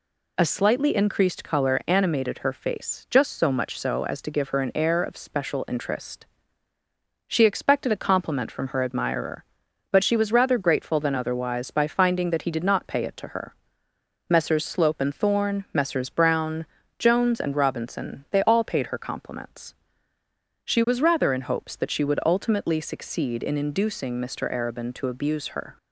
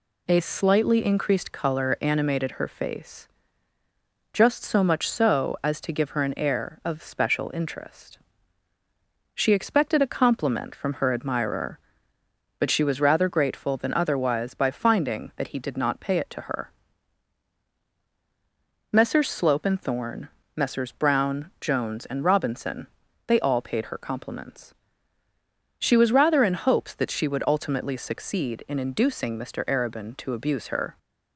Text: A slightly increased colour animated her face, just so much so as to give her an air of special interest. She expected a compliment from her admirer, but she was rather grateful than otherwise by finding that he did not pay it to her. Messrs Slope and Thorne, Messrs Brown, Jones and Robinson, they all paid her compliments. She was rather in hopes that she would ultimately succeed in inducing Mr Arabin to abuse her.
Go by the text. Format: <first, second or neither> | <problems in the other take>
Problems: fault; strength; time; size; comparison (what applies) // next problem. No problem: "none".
neither | none